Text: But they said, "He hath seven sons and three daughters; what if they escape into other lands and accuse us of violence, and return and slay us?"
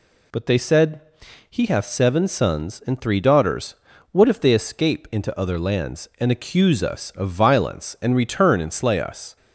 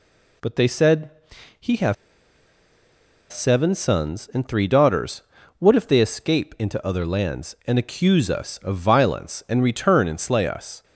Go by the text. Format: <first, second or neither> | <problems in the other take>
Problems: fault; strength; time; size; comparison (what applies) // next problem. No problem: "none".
first | pauses between "hath" and "seven"; strong; at 1.9 s; 1.3 s long